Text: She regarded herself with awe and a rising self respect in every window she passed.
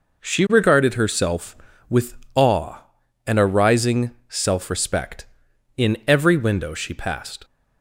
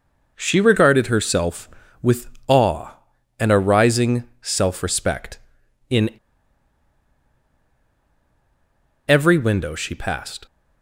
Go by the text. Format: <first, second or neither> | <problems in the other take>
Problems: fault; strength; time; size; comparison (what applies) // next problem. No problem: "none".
first | pauses between "with" and "awe"; slight; at 2.2 s; 0.20 s long; slight in the first // pauses between "in" and "every"; strong; at 6.0 s; 2.9 s long